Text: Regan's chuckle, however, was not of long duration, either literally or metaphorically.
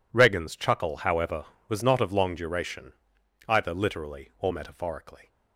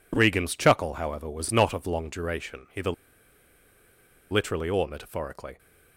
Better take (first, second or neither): first